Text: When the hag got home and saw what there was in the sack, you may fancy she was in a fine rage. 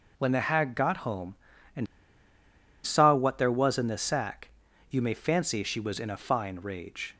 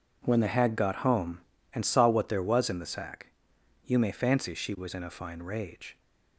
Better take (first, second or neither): second